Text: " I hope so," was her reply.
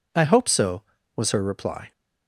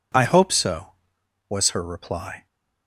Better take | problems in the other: neither | none

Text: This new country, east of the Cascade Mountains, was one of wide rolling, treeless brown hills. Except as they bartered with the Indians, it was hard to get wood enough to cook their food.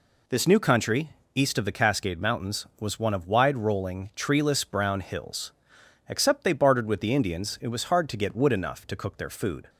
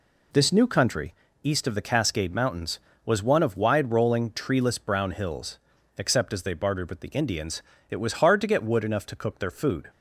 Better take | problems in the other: second | skips "as"; at 6.4 s

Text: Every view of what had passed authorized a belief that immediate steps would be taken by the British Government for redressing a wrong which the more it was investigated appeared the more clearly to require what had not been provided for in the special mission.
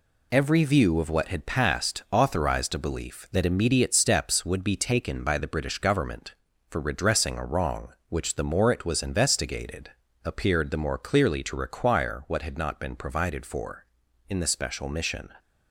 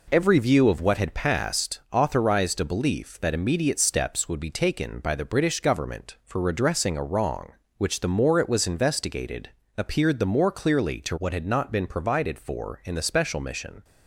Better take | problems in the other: first | pauses between "investigated" and "appeared"; slight; at 9.5 s; 0.26 s long; slight in the first // skips "require"; at 11.1 s

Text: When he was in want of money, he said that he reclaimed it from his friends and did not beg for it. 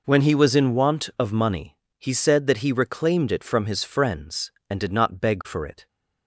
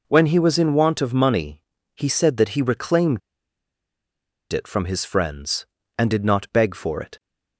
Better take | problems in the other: first | pauses between "reclaimed" and "it"; strong; at 3.2 s; 1.3 s long

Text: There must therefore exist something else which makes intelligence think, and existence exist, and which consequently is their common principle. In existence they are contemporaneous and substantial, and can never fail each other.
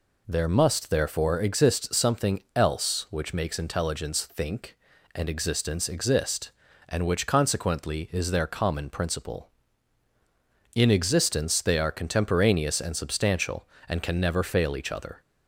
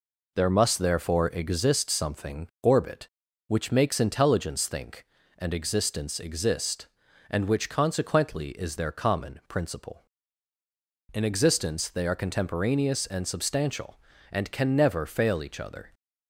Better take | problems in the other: first | says "orbit" for "else"; at 2.6 s

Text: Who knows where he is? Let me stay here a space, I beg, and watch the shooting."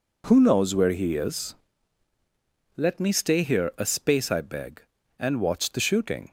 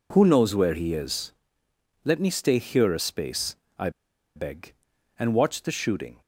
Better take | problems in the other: first | pauses between "I" and "beg"; noticeable; at 3.8 s; 0.46 s long

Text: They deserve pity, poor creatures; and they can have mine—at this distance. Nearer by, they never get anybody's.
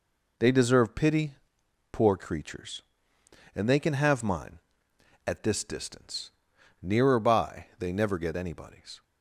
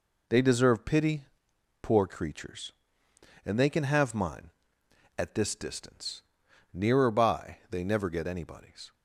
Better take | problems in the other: neither | none

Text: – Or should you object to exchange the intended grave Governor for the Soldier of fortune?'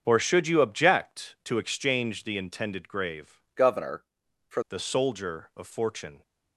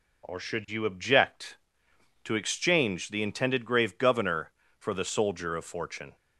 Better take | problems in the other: second | starts louder than the rest; until 1.0 s; 7 dB // changes voice from "Governor" to "for"; from 3.5 to 4.6 s; 1.1 s long

